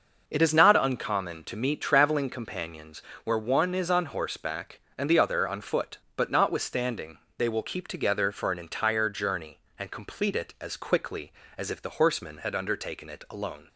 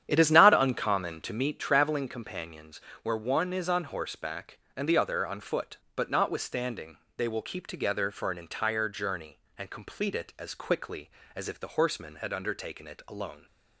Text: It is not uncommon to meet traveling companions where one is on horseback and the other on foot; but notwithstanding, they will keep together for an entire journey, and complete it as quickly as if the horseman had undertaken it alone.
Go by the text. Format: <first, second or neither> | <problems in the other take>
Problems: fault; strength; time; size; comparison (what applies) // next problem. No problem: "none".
first | starts louder than the rest; strong; until 1.5 s; 9.5 dB // pauses between "companions" and "where"; slight; at 2.8 s; 0.22 s long; slight in the first